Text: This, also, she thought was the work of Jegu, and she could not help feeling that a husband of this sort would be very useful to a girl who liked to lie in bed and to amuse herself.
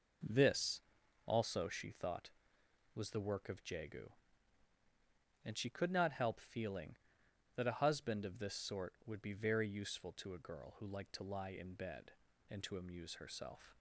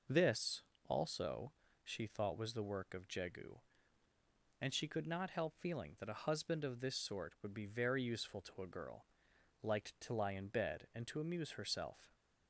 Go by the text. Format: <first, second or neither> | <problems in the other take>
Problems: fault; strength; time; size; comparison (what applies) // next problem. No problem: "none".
first | skips "who"; at 9.3 s